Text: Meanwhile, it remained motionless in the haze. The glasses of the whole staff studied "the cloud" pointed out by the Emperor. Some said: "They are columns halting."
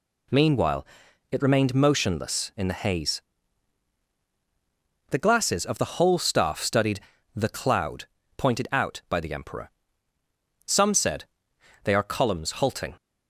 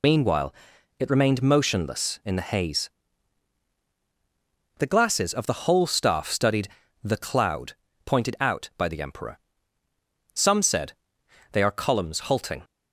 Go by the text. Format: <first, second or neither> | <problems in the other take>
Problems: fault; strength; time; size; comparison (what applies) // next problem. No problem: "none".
first | loses the start of "Meanwhile"; at 0.0 s; 60 ms // pauses between "studied" and "the"; slight; at 6.6 s; 0.34 s long; slight in the first // pauses between "cloud" and "pointed"; slight; at 7.7 s; 0.32 s long; slight in the first